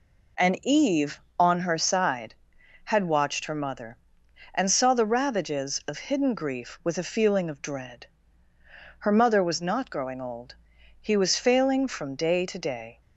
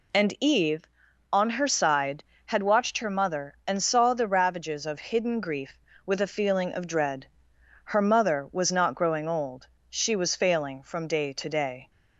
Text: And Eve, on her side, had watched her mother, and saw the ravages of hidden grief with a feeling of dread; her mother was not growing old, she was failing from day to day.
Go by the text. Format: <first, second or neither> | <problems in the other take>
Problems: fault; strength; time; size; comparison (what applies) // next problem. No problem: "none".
second | says "he" for "she"; at 11.0 s